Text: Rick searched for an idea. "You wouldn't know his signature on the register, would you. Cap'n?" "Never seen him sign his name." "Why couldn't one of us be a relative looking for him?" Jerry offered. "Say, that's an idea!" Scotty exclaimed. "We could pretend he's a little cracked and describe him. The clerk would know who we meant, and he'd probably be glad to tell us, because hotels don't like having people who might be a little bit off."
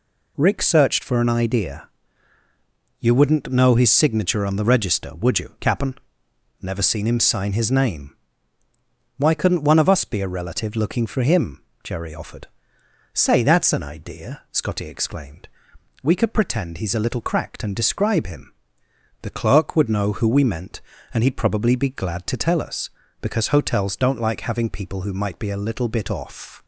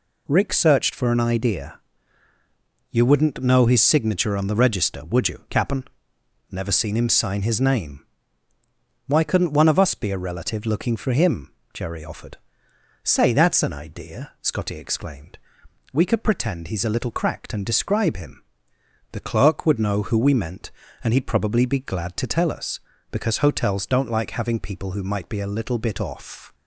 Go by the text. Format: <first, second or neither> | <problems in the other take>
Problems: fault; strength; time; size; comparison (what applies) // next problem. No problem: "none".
neither | none